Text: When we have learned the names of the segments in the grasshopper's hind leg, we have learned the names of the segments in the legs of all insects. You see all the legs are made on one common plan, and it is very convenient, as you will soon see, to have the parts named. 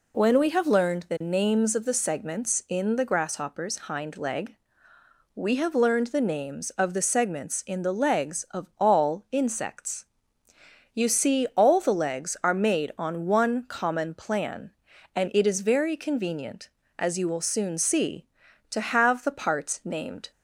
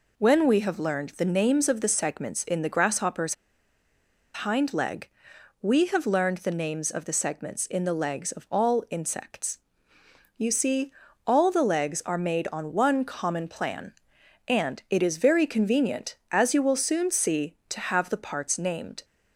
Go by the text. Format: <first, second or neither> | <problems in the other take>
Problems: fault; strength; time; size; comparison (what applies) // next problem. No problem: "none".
first | pauses between "grasshopper's" and "hind"; at 3.3 s; 1.1 s long // pauses between "see" and "all"; slight; at 10.9 s; 0.34 s long